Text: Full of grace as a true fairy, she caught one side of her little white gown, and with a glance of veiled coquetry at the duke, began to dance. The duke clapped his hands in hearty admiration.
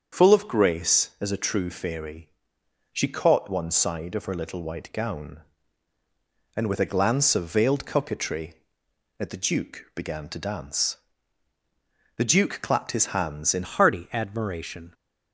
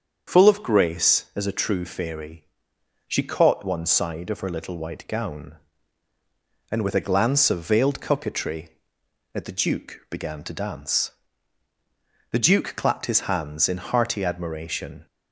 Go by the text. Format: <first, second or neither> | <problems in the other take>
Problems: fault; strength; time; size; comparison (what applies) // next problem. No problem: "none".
second | starts louder than the rest; until 1.2 s; 7 dB; also in the second // changes voice at "hearty"; from 13.6 s on; 1.3 s long